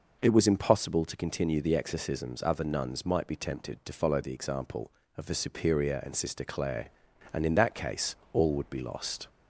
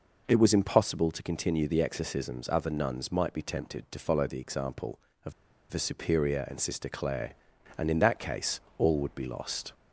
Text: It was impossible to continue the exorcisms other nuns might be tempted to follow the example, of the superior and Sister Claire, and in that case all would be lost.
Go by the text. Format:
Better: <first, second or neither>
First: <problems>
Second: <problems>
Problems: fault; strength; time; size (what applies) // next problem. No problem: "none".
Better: first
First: pauses between "case" and "all"; slight; at 8.1 s; 0.19 s long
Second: pauses between "of" and "the"; at 5.3 s; 0.38 s long // pauses between "case" and "all"; slight; at 8.5 s; 0.20 s long